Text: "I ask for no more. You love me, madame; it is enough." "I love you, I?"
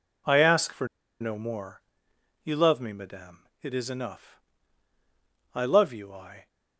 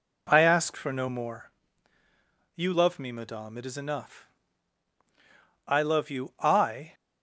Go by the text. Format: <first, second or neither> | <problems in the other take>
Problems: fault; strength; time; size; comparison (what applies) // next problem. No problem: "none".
second | pauses between "for" and "no"; slight; at 0.8 s; 0.33 s long